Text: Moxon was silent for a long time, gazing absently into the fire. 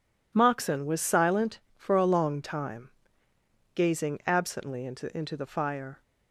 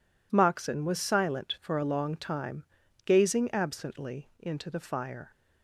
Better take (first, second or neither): second